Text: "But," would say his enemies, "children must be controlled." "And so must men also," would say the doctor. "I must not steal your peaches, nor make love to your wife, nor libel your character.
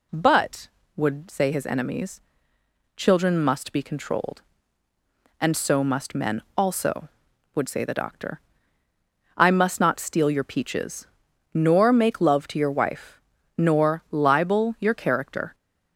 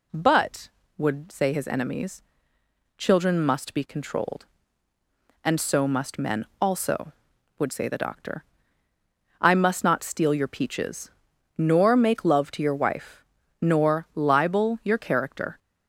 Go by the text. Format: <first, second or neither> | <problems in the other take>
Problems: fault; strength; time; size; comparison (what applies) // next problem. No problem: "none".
neither | none